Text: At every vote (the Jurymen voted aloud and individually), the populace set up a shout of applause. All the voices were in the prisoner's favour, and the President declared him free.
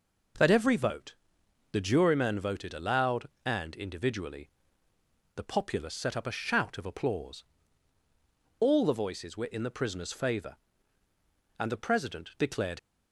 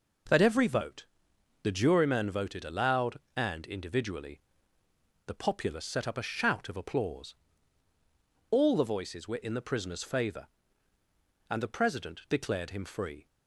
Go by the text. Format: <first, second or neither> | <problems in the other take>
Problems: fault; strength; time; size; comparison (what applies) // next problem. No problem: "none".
second | stops before "him free"; at 12.7 s